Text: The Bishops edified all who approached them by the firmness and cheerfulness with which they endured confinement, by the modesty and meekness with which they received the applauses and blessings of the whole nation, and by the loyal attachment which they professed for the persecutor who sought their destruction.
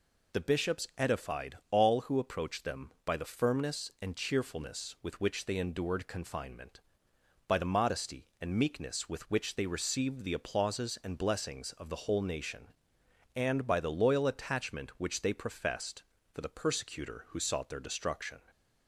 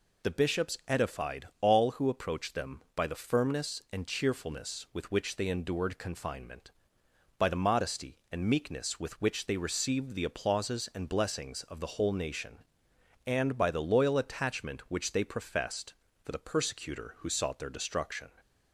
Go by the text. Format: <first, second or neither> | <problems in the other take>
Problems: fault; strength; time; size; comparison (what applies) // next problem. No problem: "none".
neither | none